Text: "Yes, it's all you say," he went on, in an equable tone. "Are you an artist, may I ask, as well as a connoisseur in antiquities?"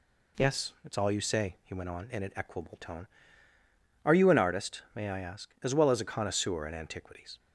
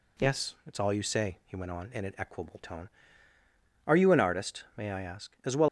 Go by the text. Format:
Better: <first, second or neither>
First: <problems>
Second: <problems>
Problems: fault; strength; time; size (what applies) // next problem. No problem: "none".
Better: first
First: none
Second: stops before "as a connoisseur in antiquities"; at 5.6 s